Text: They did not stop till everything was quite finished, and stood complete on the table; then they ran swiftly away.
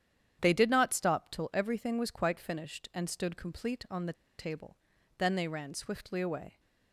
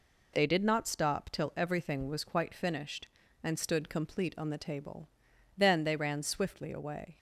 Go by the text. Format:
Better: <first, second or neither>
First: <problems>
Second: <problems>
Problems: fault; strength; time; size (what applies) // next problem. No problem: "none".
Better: second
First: starts louder than the rest; strong; until 1.4 s; 9.5 dB // pauses between "the" and "table"; slight; at 4.1 s; 0.25 s long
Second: none